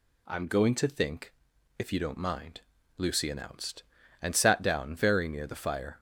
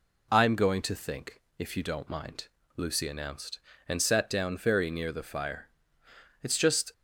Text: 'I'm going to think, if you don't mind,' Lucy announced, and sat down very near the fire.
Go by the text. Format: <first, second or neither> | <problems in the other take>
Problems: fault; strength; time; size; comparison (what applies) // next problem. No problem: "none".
first | goes on to say "It's just"; from 6.4 s on; 0.50 s long